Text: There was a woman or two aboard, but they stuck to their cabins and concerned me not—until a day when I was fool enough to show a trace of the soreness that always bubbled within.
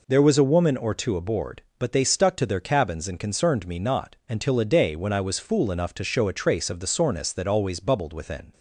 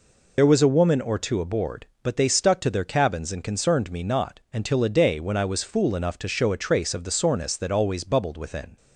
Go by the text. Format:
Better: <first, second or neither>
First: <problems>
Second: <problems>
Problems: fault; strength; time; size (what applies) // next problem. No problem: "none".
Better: first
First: none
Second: loses the start of "There"; at 0.3 s; 75 ms